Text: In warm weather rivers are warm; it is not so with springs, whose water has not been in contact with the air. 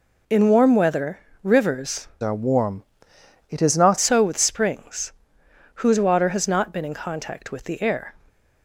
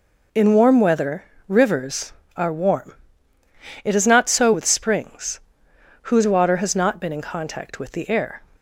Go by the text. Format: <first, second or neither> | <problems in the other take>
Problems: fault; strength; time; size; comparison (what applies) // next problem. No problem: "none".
second | pauses between "weather" and "rivers"; slight; at 1.1 s; 0.24 s long; slight in the second // changes voice from "are" to "not"; from 2.2 to 3.9 s; 1.7 s long